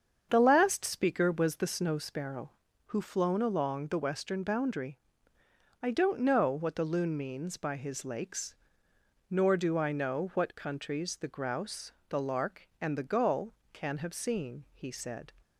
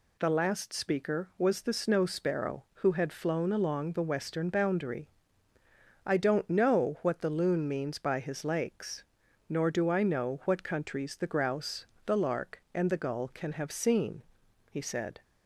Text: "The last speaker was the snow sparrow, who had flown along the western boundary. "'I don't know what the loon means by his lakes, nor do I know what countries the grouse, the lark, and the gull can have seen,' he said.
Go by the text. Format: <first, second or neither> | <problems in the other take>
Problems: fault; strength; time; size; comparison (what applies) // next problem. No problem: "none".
second | starts louder than the rest; strong; until 1.3 s; 7.5 dB // skips "had"; at 3.0 s